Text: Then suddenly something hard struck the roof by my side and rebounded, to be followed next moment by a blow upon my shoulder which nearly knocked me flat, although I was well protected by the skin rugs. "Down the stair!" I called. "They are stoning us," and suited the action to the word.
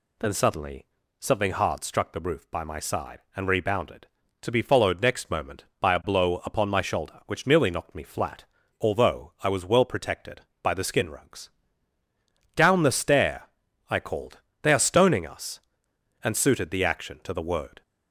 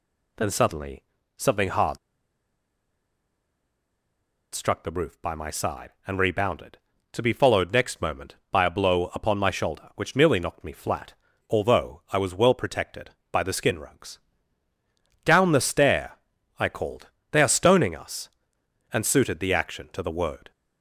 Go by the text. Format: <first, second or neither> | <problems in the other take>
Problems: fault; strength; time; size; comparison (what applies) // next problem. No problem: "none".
first | pauses between "suddenly" and "something"; slight; at 1.0 s; 0.32 s long; slight in the first // pauses between "hard" and "struck"; strong; at 1.9 s; 2.5 s long